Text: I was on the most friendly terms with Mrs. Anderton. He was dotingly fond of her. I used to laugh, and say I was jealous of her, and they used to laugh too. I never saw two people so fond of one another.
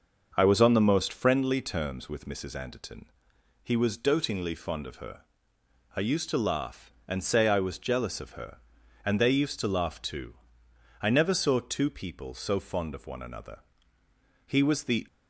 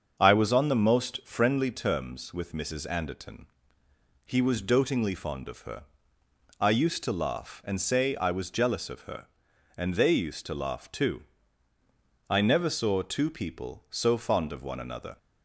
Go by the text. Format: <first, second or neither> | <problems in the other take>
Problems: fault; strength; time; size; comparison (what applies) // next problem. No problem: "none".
second | starts louder than the rest; until 1.3 s; 6.5 dB; also in the second // goes on to say "He was the"; from 14.4 s on; 0.60 s long